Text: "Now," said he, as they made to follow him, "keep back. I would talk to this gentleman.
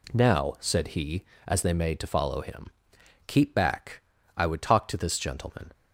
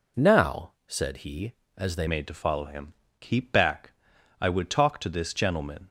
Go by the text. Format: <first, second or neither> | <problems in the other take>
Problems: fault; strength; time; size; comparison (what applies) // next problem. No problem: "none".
first | changes voice at "made"; from 2.0 s on; 3.8 s long